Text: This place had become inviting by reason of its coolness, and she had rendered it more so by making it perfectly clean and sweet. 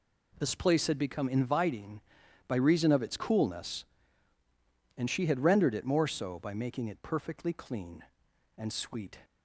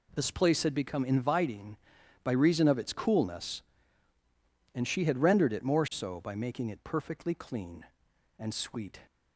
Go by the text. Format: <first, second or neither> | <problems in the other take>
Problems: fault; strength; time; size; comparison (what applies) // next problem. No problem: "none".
neither | none